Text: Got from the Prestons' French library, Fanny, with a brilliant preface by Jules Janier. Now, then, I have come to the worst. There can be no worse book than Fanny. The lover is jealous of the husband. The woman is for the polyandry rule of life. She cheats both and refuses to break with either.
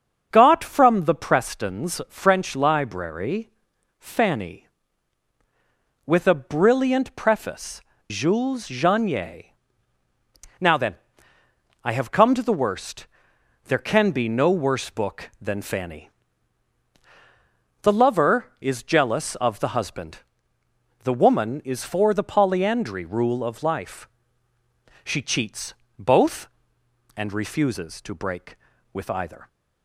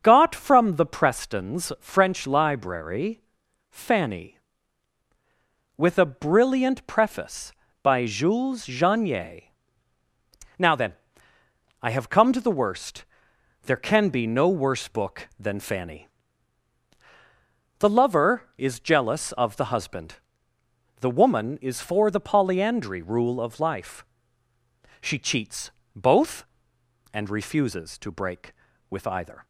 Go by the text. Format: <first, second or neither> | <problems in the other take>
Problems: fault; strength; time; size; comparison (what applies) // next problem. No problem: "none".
second | starts louder than the rest; until 1.3 s; 6.5 dB; also in the second // skips "by"; at 7.9 s // pauses between "cheats" and "both"; slight; at 25.7 s; 0.24 s long; slight in the second